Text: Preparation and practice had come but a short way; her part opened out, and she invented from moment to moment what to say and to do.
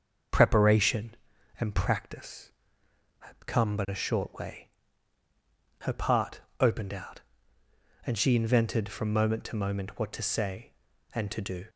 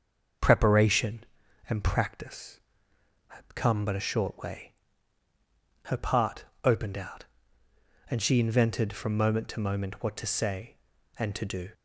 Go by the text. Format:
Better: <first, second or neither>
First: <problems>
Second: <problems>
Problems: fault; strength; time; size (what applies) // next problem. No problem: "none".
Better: neither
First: starts louder than the rest; until 1.7 s; 6.5 dB // pauses between "part" and "opened"; slight; at 6.4 s; 0.20 s long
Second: starts louder than the rest; until 1.8 s; 6.5 dB // pauses between "part" and "opened"; slight; at 6.4 s; 0.20 s long